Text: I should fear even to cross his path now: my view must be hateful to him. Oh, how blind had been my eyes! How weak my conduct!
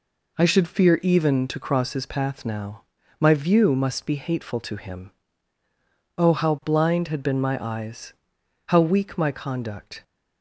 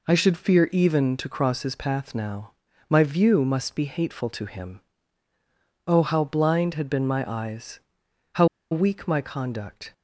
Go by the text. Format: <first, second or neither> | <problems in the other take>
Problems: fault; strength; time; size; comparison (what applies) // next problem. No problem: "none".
first | pauses between "How" and "weak"; slight; at 8.4 s; 0.25 s long